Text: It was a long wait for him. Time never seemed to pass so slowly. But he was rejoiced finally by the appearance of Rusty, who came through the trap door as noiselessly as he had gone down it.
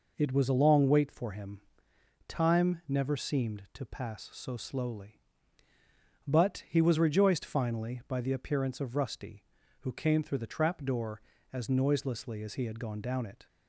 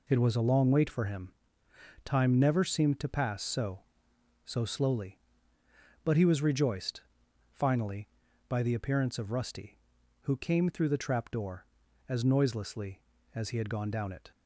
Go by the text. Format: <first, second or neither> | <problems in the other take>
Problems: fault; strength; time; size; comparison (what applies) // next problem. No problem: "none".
first | says "so" twice; at 4.4 s // pauses between "rejoiced" and "finally"; noticeable; at 7.0 s; 0.50 s long